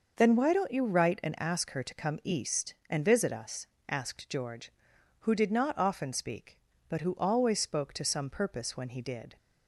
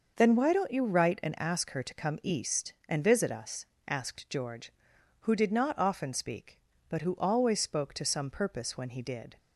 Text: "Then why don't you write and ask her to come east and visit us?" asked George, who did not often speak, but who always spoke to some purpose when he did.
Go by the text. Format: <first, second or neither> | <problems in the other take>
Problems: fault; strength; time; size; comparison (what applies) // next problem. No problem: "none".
neither | none